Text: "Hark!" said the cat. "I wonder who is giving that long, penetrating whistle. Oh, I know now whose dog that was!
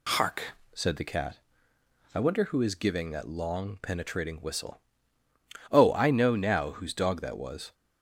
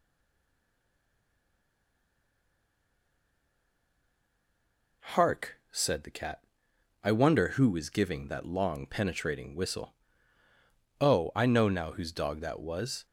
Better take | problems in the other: first | stays silent before the first word; strong; until 5.0 s; 5.0 s long

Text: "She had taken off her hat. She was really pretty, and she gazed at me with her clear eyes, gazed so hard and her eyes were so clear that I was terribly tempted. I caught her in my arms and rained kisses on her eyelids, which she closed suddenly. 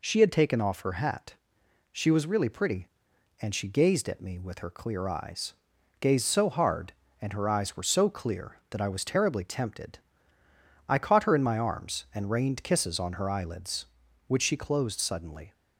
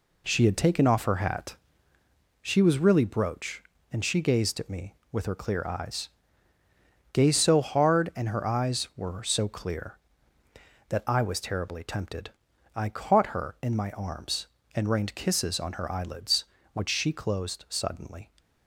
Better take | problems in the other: first | says "brooch" for "pretty"; at 3.0 s

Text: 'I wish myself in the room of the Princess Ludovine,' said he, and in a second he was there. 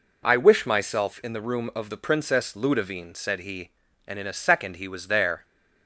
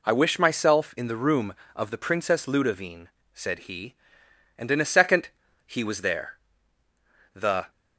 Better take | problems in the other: first | pauses between "second" and "he"; at 5.2 s; 0.40 s long // goes on to say "The"; slight; from 7.3 s on; 0.36 s long

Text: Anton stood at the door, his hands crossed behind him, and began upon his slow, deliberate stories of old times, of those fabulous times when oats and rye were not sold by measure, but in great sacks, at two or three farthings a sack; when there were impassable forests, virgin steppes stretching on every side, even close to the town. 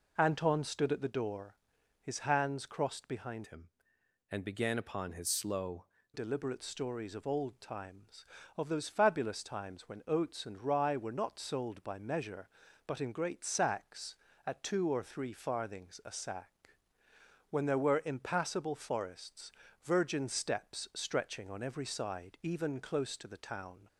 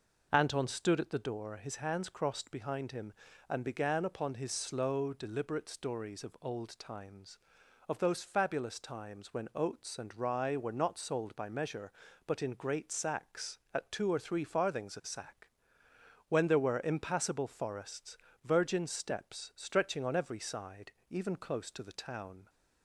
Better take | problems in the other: second | changes voice from "him" to "slow"; from 3.4 to 5.8 s; 2.4 s long

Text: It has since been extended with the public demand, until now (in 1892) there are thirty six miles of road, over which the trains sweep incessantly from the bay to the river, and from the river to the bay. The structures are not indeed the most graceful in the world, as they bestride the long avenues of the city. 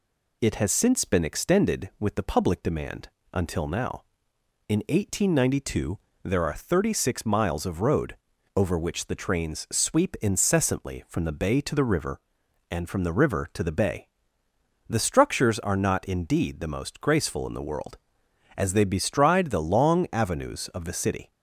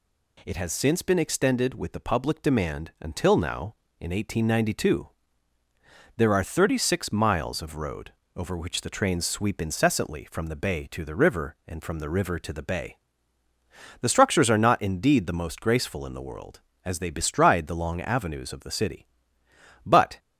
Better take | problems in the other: first | goes on to say "But"; slight; from 19.8 s on; 0.34 s long

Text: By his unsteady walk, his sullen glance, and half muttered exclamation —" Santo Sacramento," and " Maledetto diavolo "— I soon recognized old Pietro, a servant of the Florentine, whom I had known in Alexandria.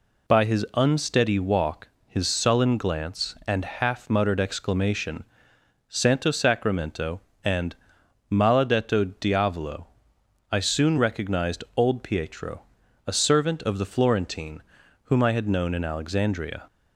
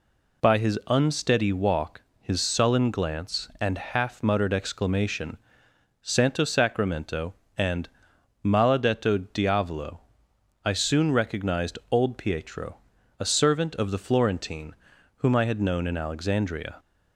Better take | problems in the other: neither | none

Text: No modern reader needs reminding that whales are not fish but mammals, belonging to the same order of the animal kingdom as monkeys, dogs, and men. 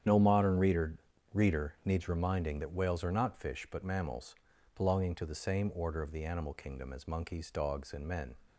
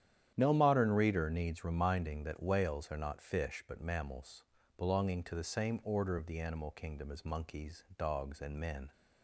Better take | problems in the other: second | starts louder than the rest; strong; until 1.4 s; 9 dB; strong in the second // says "reader" twice; at 1.3 s

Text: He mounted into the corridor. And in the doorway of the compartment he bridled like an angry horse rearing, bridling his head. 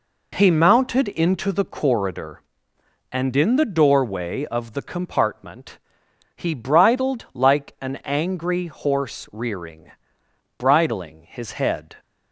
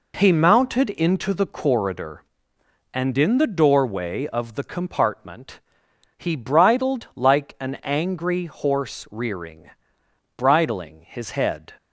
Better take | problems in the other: neither | pauses between "compartment" and "he"; noticeable; the same in both

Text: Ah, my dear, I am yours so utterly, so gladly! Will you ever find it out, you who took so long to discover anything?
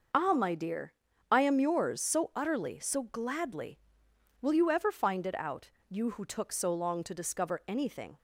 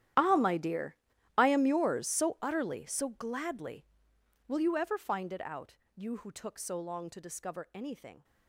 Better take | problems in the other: first | gets quieter; strong; throughout; 19 dB

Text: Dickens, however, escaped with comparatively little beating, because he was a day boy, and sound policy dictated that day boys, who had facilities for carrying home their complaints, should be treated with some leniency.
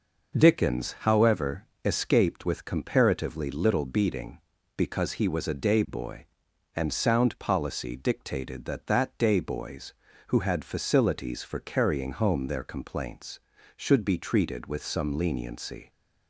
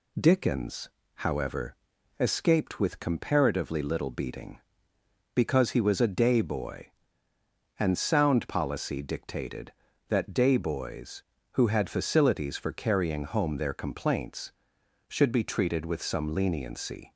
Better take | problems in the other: second | says "that" twice; at 8.8 s

